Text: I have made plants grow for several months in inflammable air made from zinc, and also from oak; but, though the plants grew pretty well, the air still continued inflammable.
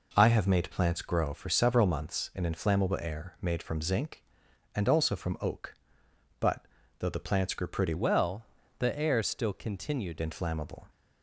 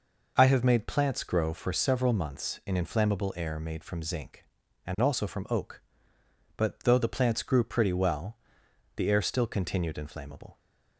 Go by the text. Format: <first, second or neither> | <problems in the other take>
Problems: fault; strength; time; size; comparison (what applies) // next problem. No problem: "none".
second | changes voice from "well" to "continued"; from 7.9 to 10.2 s; 2.3 s long